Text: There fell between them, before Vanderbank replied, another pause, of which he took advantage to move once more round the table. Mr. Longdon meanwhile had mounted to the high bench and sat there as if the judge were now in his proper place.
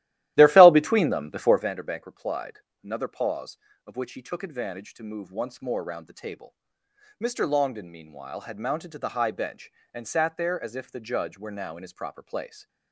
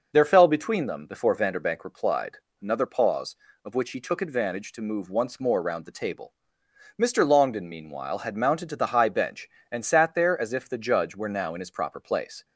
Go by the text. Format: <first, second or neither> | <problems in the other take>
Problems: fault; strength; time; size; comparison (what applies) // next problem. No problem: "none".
second | starts louder than the rest; strong; until 1.7 s; 14.5 dB